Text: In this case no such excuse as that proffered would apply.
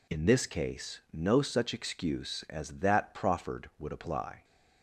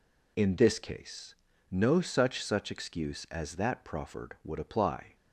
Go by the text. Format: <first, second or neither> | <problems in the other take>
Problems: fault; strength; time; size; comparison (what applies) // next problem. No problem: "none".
first | pauses between "case" and "no"; at 1.3 s; 0.38 s long // says "such" twice; at 2.4 s